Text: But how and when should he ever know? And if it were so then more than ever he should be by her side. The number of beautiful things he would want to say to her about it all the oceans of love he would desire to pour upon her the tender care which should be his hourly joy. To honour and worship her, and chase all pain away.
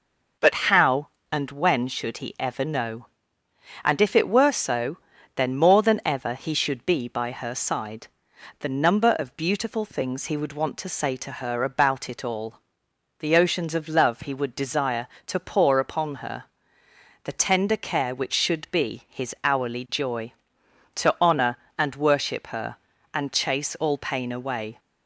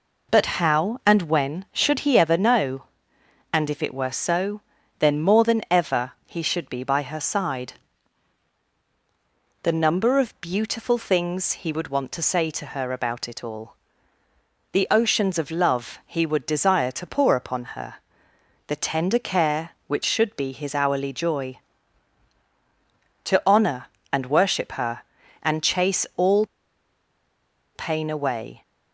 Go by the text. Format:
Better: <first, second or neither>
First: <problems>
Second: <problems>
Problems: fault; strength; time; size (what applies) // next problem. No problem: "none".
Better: first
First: pauses between "so" and "then"; at 4.9 s; 0.38 s long // pauses between "all" and "the"; noticeable; at 12.5 s; 0.60 s long // pauses between "her" and "the"; noticeable; at 16.4 s; 0.80 s long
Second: pauses between "so" and "then"; at 4.6 s; 0.38 s long // pauses between "all" and "the"; noticeable; at 13.7 s; 0.98 s long // pauses between "her" and "the"; noticeable; at 17.9 s; 0.72 s long // pauses between "all" and "pain"; strong; at 26.4 s; 1.2 s long